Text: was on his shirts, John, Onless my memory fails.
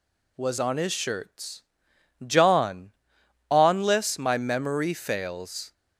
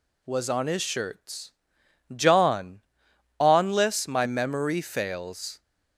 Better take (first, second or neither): neither